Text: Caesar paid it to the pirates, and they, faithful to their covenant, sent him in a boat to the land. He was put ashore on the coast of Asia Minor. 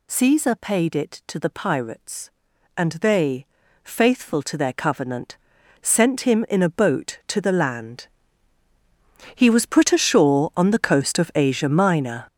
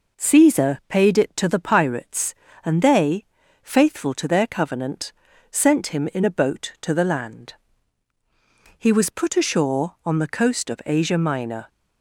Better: second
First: gets louder; strong; throughout; 10.5 dB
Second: none

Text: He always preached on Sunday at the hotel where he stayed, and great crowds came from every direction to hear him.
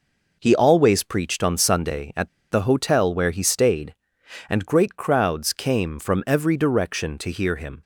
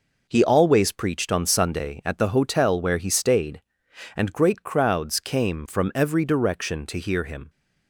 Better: second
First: pauses between "at" and "the"; slight; at 2.2 s; 0.22 s long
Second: none

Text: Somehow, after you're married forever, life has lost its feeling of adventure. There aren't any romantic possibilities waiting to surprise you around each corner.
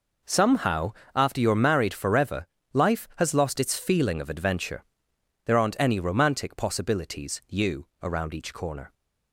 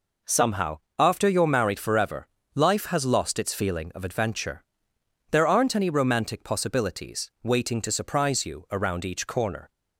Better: second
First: skips "waiting to surprise"; at 7.4 s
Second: none

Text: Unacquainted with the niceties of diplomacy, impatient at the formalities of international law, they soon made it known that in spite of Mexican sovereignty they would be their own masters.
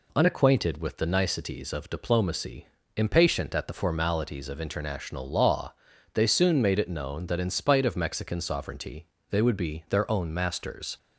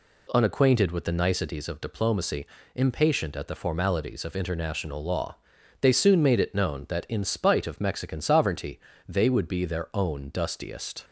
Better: first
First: pauses between "sovereignty" and "they"; slight; at 9.0 s; 0.22 s long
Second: pauses between "sovereignty" and "they"; slight; at 8.7 s; 0.30 s long // says "dustiest" for "masters"; at 10.3 s

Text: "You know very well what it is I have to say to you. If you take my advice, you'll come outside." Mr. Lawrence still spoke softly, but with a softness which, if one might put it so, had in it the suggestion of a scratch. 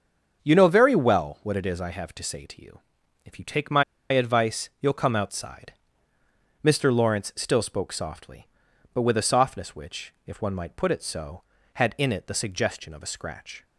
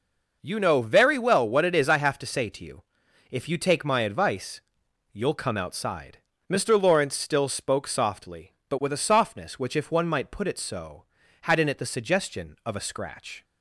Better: second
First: starts louder than the rest; until 1.4 s; 7 dB // pauses between "my" and "advice"; slight; at 3.8 s; 0.28 s long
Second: none

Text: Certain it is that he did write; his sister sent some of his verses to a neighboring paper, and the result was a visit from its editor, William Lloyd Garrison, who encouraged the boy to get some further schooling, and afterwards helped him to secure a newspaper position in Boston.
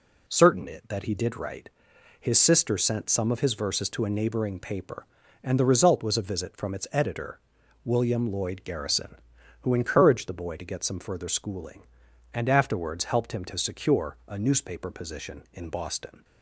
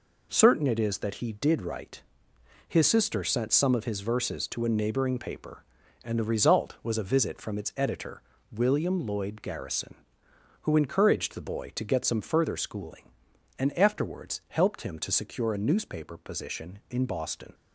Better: second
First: skips "is"; at 0.8 s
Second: none

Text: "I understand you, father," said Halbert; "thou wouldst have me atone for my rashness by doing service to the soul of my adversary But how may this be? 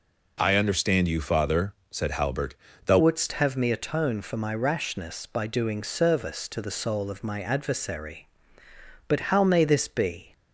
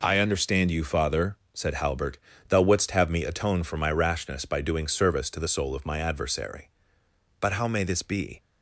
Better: second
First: changes voice at "wouldst"; from 2.9 s on; 7.4 s long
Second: none

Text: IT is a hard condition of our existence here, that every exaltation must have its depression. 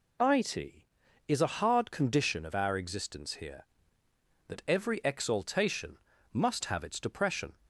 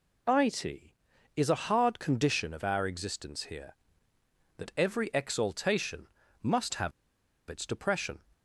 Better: first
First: pauses between "exaltation" and "must"; slight; at 5.9 s; 0.36 s long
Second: pauses between "exaltation" and "must"; slight; at 6.0 s; 0.36 s long // pauses between "have" and "its"; noticeable; at 6.9 s; 0.59 s long

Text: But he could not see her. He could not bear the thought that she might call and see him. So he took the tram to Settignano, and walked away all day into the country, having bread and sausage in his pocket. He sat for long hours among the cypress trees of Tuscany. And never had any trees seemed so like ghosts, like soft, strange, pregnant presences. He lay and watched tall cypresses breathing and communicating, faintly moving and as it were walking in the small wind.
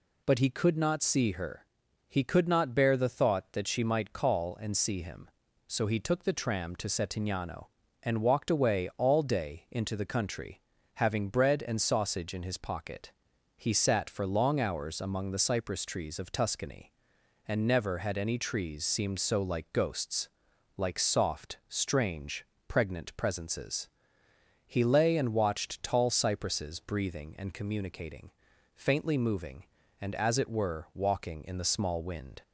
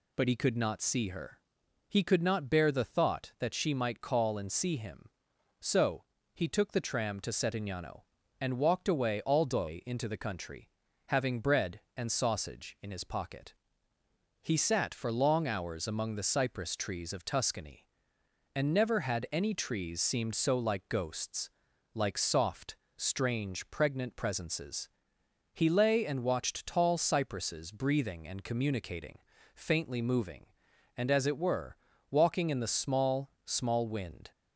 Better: first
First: none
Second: pauses between "So" and "he"; slight; at 6.0 s; 0.30 s long // pauses between "were" and "walking"; slight; at 31.7 s; 0.34 s long // says "small" twice; at 33.4 s

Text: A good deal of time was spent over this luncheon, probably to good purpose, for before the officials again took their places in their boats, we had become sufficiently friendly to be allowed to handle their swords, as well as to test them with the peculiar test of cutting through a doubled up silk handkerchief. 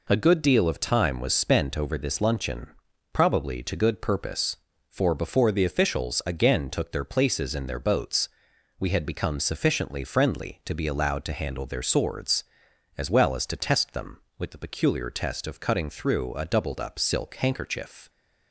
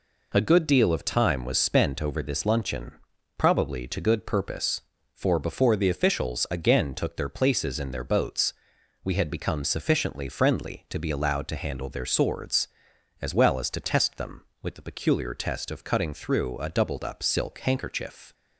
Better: neither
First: none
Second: none

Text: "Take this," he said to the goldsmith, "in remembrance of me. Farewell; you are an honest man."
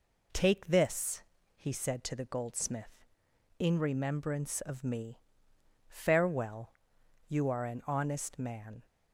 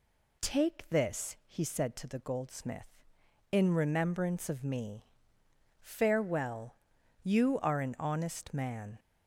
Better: neither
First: none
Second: none

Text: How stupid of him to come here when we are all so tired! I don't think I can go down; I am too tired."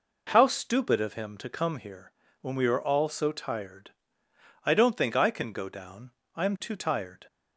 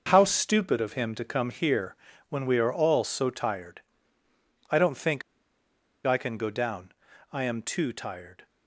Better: first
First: pauses between "here" and "when"; slight; at 2.1 s; 0.30 s long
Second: starts louder than the rest; noticeable; until 1.0 s; 6 dB // pauses between "here" and "when"; slight; at 1.9 s; 0.32 s long // pauses between "think" and "I"; noticeable; at 5.2 s; 0.84 s long

